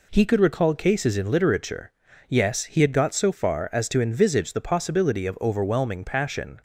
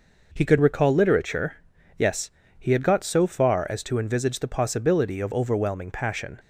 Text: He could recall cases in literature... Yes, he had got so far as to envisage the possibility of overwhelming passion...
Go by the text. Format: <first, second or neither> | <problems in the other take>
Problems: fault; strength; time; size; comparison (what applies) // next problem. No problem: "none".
first | skips "cases in"; at 0.9 s